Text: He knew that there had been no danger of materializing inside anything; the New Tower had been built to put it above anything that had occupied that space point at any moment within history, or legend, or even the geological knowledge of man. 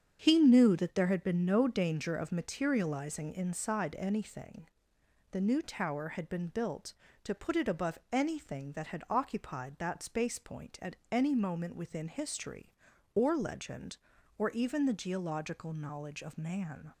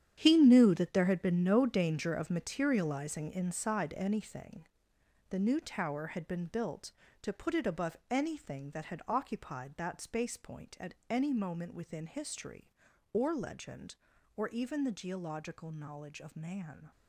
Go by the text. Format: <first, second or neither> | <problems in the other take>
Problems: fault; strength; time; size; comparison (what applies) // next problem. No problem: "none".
first | gets quieter; strong; throughout; 12.5 dB // starts louder than the rest; strong; until 1.2 s; 9.5 dB; strong in the first